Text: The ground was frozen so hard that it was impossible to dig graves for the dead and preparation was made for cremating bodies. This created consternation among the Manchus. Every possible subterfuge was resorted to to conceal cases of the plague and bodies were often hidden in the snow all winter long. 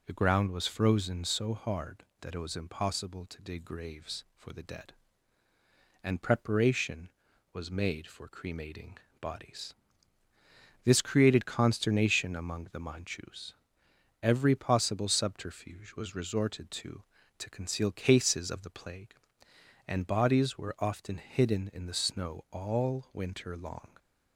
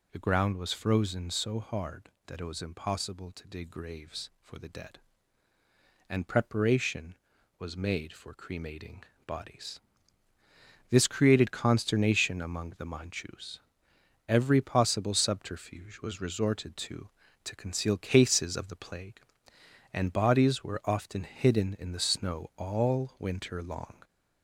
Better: first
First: pauses between "cremating" and "bodies"; slight; at 8.9 s; 0.22 s long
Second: gets louder; slight; throughout; 3 dB // pauses between "cremating" and "bodies"; slight; at 9.0 s; 0.22 s long

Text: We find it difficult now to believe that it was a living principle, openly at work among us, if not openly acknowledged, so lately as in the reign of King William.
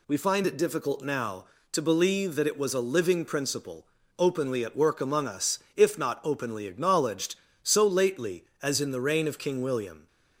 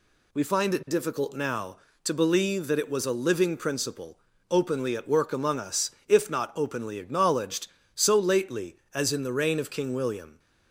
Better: neither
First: none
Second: none

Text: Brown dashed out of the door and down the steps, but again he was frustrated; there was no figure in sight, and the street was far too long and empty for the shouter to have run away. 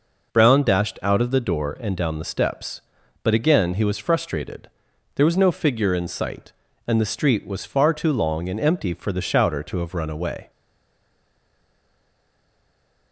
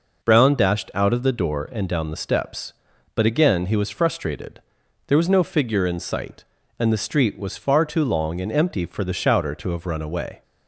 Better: second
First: stays silent after the last word; strong; from 10.4 s on; 2.7 s long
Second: none

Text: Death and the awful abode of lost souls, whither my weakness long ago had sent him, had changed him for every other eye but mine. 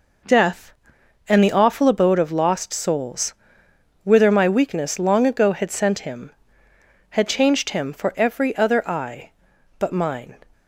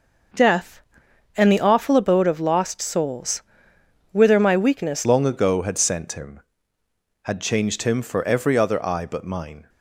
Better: first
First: none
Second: changes voice at "long"; from 5.0 s on; 4.6 s long

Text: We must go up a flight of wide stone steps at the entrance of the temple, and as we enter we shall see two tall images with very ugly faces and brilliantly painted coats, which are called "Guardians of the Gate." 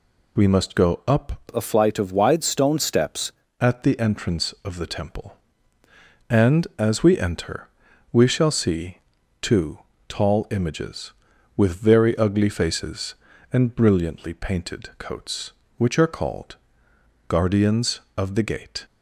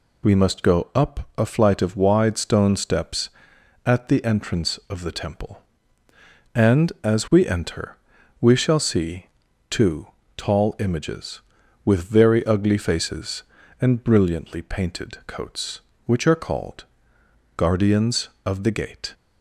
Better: second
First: changes voice from "a" to "steps"; from 1.5 to 3.3 s; 1.8 s long // pauses between "enter" and "we"; noticeable; at 7.6 s; 0.46 s long // pauses between "see" and "two"; at 8.9 s; 0.42 s long // pauses between "two" and "tall"; slight; at 9.7 s; 0.28 s long // pauses between "called" and "Guardians"; noticeable; at 16.5 s; 0.72 s long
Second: pauses between "enter" and "we"; noticeable; at 7.9 s; 0.46 s long // pauses between "see" and "two"; at 9.2 s; 0.42 s long // pauses between "two" and "tall"; slight; at 10.0 s; 0.28 s long // pauses between "called" and "Guardians"; noticeable; at 16.8 s; 0.72 s long

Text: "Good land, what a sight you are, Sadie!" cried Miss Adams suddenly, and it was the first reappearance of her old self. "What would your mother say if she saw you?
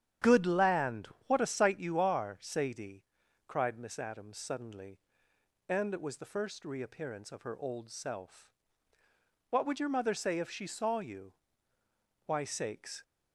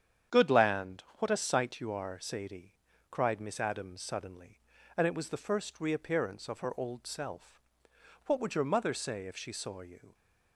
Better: second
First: starts louder than the rest; strong; until 1.4 s; 9.5 dB // goes on to say "Why sakes"; noticeable; from 12.2 s on; 0.76 s long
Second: starts louder than the rest; strong; until 1.4 s; 8.5 dB

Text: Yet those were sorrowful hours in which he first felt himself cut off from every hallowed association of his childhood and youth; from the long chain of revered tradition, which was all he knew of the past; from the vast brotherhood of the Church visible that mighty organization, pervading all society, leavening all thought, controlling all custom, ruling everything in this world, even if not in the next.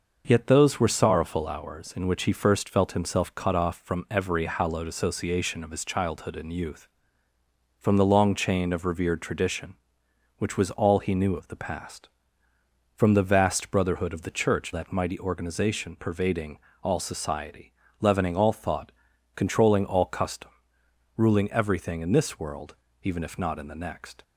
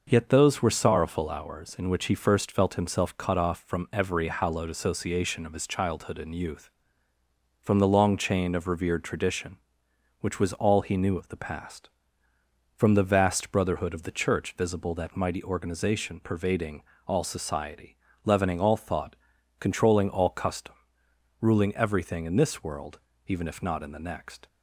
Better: second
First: skips "visible"; at 14.7 s // pauses between "pervading" and "all"; slight; at 16.5 s; 0.26 s long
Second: pauses between "pervading" and "all"; slight; at 16.8 s; 0.26 s long

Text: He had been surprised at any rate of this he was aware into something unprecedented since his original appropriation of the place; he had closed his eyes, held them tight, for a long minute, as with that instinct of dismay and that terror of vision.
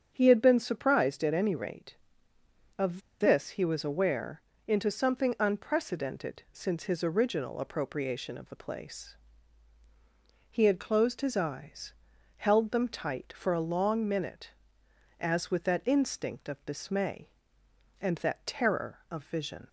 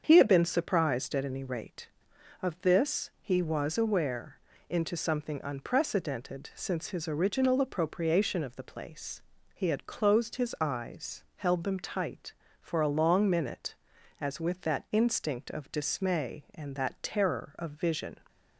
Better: second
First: starts louder than the rest; strong; until 1.1 s; 8 dB // pauses between "of" and "this"; slight; at 3.0 s; 0.20 s long // pauses between "aware" and "into"; slight; at 4.3 s; 0.26 s long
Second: starts louder than the rest; strong; until 1.0 s; 7 dB // pauses between "aware" and "into"; slight; at 4.3 s; 0.32 s long

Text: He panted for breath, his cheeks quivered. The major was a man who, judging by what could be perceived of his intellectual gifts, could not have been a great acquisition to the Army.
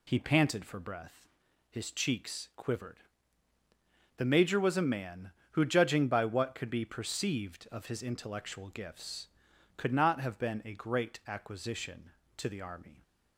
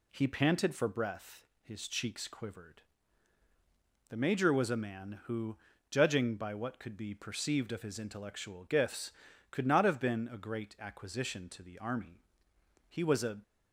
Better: first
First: none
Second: goes on to say "He was a"; from 12.8 s on; 0.52 s long

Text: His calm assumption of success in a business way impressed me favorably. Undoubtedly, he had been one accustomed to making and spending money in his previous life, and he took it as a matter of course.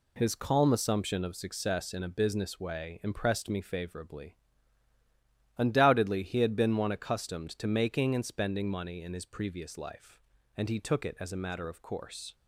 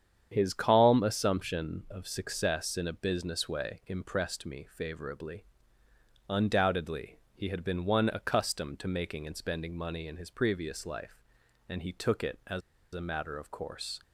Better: first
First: none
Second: starts louder than the rest; strong; until 1.3 s; 8.5 dB // pauses between "as" and "a"; slight; at 12.6 s; 0.32 s long

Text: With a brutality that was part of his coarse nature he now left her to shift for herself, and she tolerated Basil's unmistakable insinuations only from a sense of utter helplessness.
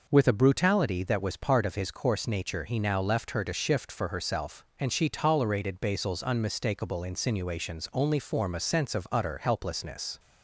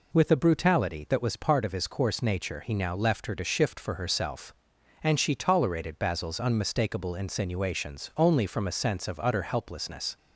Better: second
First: says "form" for "from"; at 8.1 s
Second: none

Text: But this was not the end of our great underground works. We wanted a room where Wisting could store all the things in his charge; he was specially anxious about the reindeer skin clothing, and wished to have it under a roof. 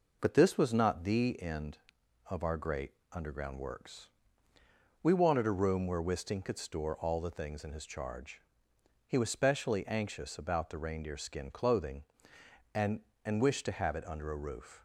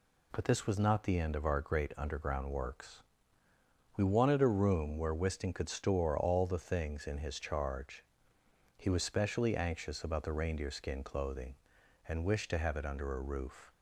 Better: second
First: pauses between "great" and "underground"; slight; at 2.9 s; 0.18 s long // says "and" twice; at 13.2 s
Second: none

